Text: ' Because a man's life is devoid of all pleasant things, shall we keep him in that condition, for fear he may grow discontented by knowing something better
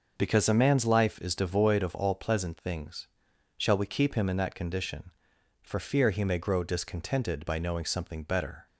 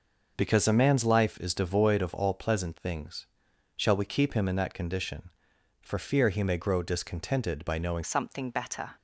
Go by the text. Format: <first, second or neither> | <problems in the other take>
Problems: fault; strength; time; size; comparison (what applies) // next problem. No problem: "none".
first | changes voice at "something"; from 8.0 s on; 0.9 s long